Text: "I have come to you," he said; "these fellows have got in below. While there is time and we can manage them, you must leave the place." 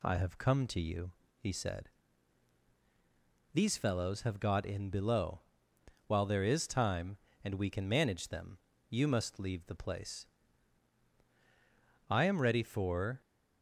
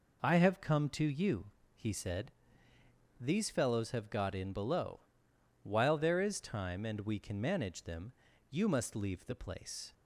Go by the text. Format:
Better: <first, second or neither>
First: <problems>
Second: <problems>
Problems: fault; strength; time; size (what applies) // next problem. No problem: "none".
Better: second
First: goes on to say "I am ready for"; noticeable; from 12.0 s on; 1.1 s long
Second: none